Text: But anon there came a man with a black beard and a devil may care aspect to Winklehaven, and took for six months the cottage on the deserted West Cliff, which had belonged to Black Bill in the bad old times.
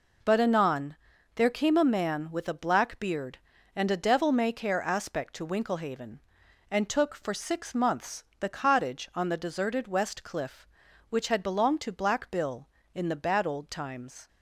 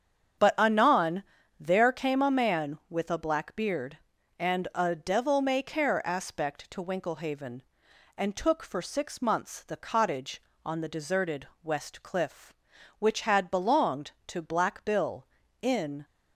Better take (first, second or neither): first